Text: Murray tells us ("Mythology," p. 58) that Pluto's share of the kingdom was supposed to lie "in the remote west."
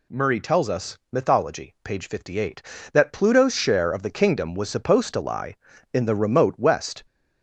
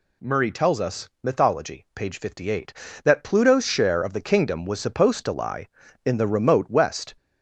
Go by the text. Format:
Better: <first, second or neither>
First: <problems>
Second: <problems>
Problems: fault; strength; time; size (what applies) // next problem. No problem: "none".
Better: neither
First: none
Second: none